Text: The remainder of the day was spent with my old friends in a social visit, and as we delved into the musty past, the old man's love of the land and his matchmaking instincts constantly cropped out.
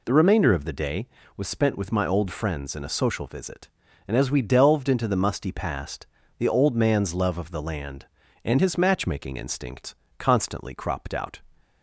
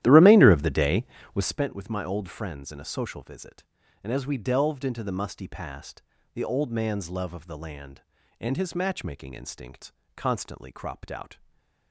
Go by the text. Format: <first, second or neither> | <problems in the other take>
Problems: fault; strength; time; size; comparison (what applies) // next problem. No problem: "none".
first | starts louder than the rest; strong; until 1.6 s; 13 dB // pauses between "instincts" and "constantly"; slight; at 9.9 s; 0.24 s long; slight in the first // stays silent after the last word; slight; from 11.3 s on; 0.6 s long